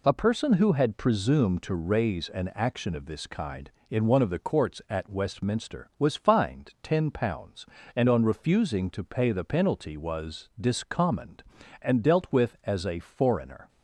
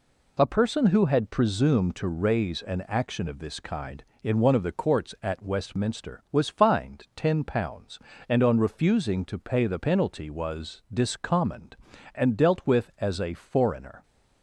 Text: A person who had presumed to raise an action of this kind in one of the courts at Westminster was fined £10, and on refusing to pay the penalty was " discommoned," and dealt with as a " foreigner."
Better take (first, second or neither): neither